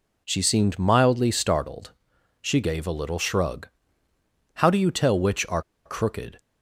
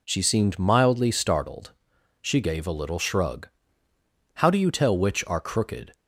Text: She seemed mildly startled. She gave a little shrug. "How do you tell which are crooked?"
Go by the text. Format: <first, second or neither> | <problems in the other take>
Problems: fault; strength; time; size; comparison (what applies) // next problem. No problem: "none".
second | pauses between "are" and "crooked"; slight; at 5.6 s; 0.24 s long